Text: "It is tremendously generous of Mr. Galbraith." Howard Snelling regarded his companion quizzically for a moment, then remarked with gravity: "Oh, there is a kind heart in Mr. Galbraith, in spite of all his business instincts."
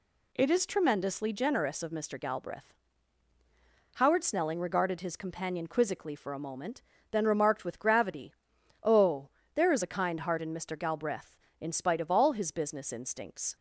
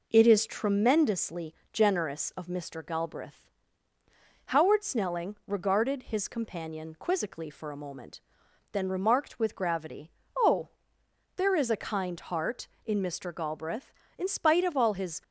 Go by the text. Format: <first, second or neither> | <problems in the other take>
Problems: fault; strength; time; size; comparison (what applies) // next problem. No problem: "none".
first | pauses between "tremendously" and "generous"; slight; at 1.5 s; 0.20 s long // stops before "business instincts"; at 15.2 s